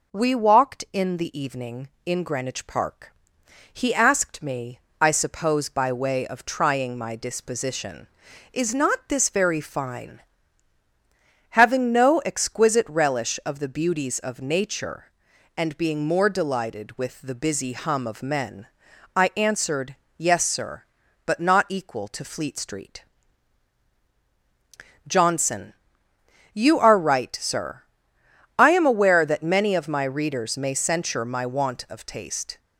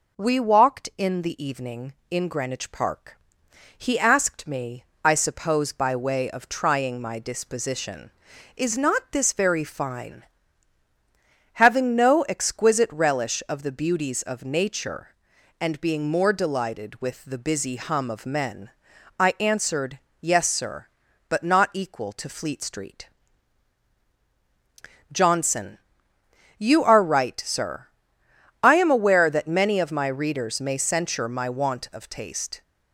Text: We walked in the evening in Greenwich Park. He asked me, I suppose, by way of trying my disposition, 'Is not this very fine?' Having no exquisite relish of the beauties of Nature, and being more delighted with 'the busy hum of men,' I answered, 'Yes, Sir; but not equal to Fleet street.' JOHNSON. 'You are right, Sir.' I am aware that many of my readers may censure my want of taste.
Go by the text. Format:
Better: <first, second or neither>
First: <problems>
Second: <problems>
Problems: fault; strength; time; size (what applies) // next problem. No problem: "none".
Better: neither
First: none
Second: none